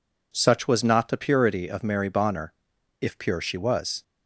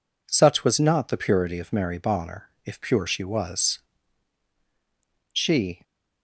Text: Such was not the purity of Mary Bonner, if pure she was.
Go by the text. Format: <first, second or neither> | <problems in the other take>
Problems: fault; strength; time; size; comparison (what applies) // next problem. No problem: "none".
first | goes on to say "She"; from 5.3 s on; 0.50 s long